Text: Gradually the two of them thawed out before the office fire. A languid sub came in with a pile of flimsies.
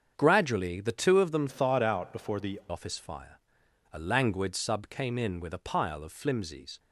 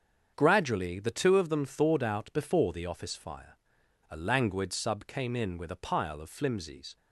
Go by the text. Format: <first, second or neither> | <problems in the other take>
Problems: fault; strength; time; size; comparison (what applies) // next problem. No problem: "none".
second | starts louder than the rest; strong; until 1.1 s; 7 dB; strong in the second // changes voice from "thawed" to "the"; from 1.4 to 2.5 s; 1.1 s long